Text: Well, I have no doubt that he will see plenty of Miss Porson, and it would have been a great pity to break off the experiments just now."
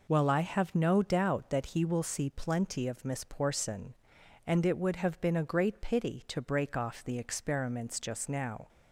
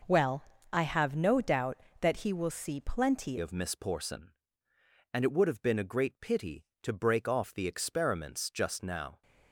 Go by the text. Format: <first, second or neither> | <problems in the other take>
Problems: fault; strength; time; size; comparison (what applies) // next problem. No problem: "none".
first | changes voice at "of"; from 3.3 s on; 5.9 s long